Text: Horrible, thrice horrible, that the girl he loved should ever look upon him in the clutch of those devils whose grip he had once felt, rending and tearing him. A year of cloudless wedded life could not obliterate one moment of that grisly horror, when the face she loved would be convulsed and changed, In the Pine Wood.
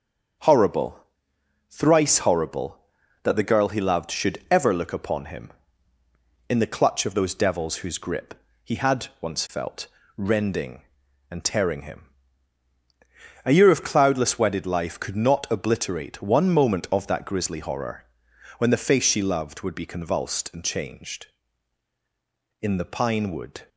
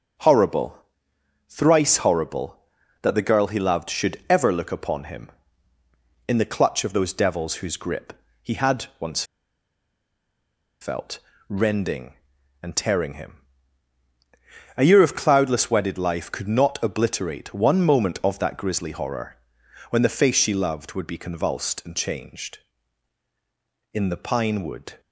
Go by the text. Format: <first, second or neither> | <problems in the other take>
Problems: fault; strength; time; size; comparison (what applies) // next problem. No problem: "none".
first | starts louder than the rest; until 1.8 s; 6.5 dB; also in the first // pauses between "grip" and "he"; slight; at 8.1 s; 0.30 s long; slight in the first // pauses between "once" and "felt"; strong; at 9.2 s; 1.5 s long